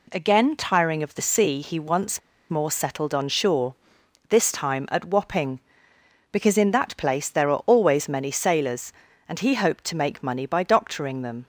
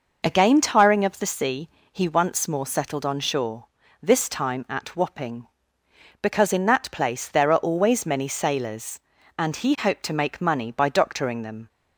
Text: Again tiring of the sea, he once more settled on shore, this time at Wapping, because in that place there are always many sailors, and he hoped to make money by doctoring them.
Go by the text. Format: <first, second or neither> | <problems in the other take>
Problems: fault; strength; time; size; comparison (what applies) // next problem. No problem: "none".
second | pauses between "once" and "more"; slight; at 2.1 s; 0.31 s long